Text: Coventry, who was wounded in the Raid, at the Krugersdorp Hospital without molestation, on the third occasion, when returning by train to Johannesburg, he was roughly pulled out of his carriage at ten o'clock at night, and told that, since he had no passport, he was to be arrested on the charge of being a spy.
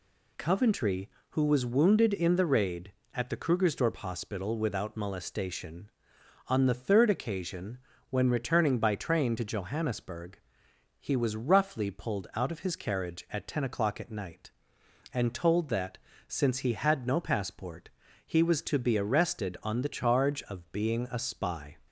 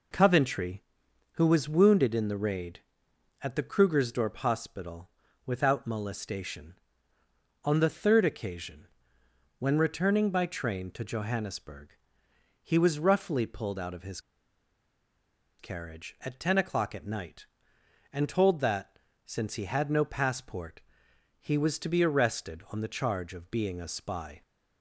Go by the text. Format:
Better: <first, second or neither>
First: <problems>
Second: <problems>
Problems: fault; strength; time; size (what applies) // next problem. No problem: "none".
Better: first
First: none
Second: pauses between "Hospital" and "without"; at 5.0 s; 0.38 s long // pauses between "his" and "carriage"; strong; at 14.2 s; 1.3 s long